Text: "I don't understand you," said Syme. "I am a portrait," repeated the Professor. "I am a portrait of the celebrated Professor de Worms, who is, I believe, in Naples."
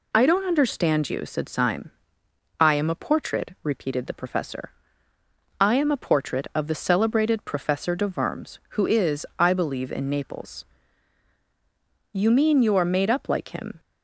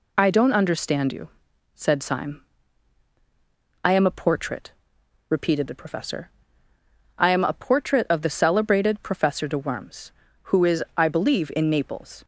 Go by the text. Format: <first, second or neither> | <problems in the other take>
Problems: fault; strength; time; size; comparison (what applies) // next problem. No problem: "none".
second | goes on to say "You mean you are made up like him"; strong; from 12.1 s on; 1.6 s long